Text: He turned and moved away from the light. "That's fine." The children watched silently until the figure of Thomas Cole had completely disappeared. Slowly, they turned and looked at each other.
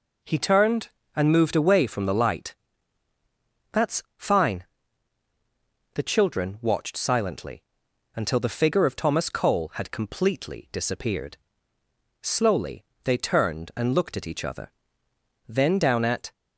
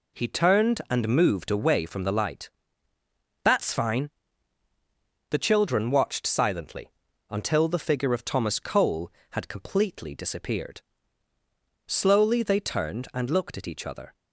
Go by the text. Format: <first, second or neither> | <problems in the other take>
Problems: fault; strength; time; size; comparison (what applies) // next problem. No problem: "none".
second | pauses between "silently" and "until"; noticeable; at 7.6 s; 0.54 s long; also in the second // goes on to say "Then down at"; noticeable; from 15.4 s on; 0.84 s long